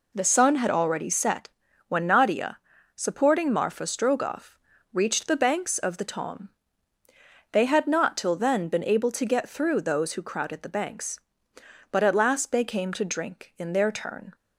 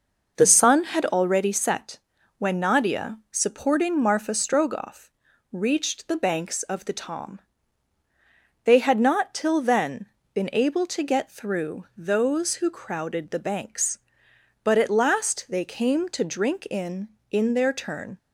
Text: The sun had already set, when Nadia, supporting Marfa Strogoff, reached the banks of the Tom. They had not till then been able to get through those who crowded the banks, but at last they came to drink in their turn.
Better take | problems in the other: first | pauses between "then" and "been"; slight; at 10.0 s; 0.26 s long // says "in" twice; at 17.3 s

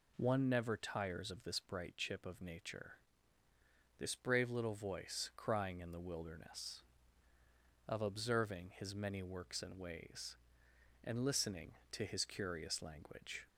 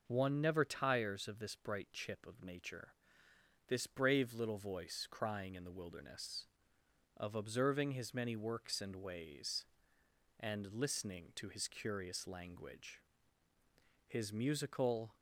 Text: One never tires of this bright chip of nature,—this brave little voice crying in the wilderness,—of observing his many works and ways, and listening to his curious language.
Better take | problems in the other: first | goes on to say "His musical"; noticeable; from 14.0 s on; 1.0 s long

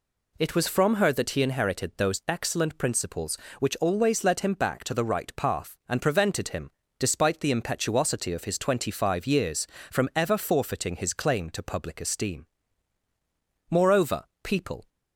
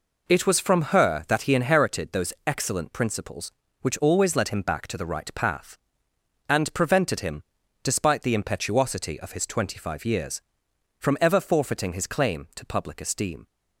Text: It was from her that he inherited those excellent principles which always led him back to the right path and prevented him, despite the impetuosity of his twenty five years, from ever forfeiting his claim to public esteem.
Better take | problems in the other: second | goes on to say "Moreover people"; noticeable; from 13.7 s on; 1.1 s long

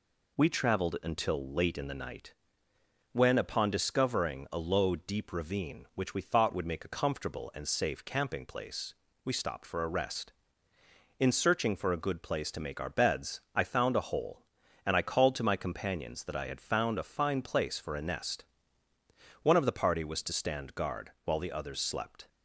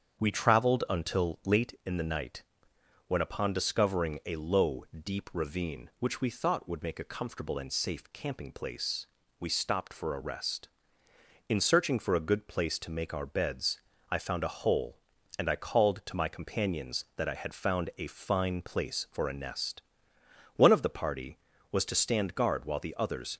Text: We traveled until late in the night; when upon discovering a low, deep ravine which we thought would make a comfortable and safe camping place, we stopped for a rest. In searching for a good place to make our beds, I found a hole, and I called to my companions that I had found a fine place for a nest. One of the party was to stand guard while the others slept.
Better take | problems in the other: first | starts louder than the rest; strong; until 1.2 s; 7.5 dB // stops before "slept"; at 23.3 s

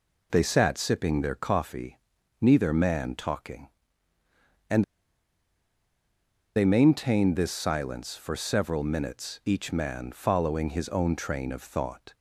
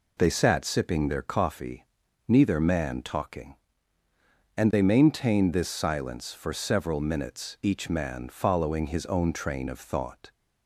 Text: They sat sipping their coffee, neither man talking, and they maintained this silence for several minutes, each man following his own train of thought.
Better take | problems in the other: second | pauses between "and" and "they"; strong; at 4.8 s; 1.7 s long

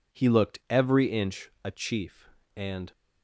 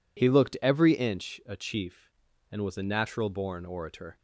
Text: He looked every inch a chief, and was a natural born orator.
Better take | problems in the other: second | stops before "was a natural born orator"; at 2.9 s

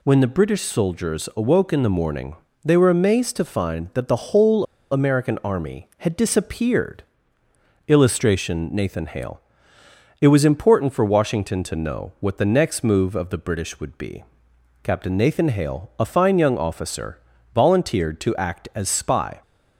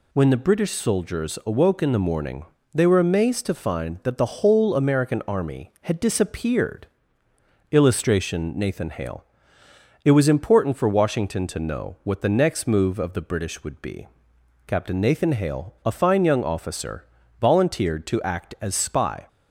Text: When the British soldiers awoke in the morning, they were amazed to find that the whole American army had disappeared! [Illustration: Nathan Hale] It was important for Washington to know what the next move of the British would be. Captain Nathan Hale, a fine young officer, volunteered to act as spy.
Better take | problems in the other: second | pauses between "whole" and "American"; slight; at 4.6 s; 0.26 s long // pauses between "Hale" and "It"; noticeable; at 9.3 s; 0.80 s long; noticeable in the second

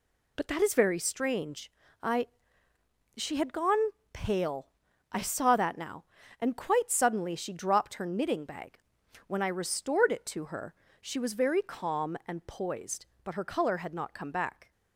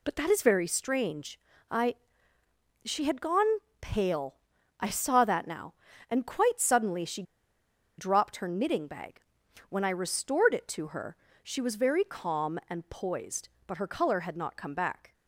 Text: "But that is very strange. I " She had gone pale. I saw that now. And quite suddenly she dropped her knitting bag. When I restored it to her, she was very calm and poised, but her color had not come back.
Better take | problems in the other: first | pauses between "gone" and "pale"; slight; at 3.5 s; 0.20 s long; slight in the first // pauses between "she" and "dropped"; noticeable; at 7.2 s; 0.75 s long

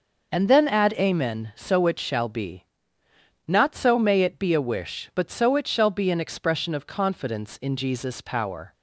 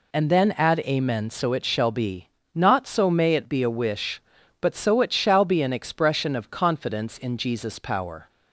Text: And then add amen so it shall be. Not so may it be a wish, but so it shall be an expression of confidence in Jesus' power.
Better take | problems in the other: neither | none

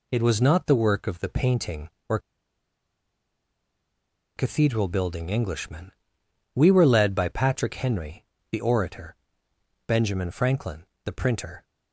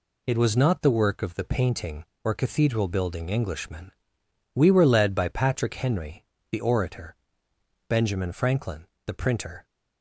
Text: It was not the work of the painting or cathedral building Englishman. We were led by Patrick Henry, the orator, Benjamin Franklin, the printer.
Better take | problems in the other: second | pauses between "or" and "cathedral"; strong; at 2.1 s; 2.1 s long

